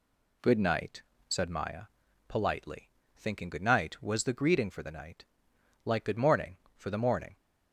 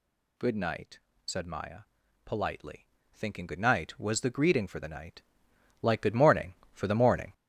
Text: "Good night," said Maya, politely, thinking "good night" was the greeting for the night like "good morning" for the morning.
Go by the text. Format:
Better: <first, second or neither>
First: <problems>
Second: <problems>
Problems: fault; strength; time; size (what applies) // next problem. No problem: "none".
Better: first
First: pauses between "night" and "like"; noticeable; at 5.2 s; 0.58 s long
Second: gets louder; strong; throughout; 7 dB // pauses between "night" and "like"; noticeable; at 5.2 s; 0.58 s long